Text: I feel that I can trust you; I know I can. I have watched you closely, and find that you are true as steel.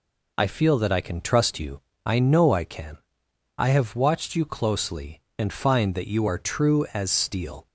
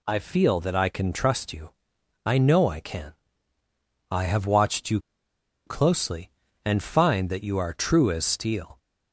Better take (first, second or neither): first